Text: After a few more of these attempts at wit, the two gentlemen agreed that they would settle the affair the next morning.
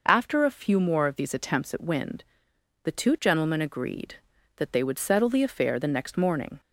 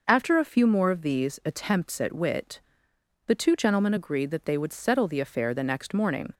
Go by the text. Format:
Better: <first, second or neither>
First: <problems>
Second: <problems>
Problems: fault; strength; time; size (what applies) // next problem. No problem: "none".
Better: second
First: says "wind" for "wit"; at 1.8 s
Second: none